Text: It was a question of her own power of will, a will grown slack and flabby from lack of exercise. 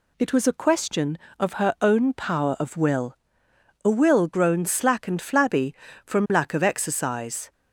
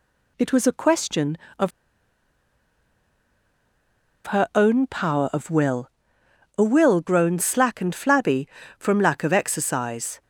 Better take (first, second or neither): first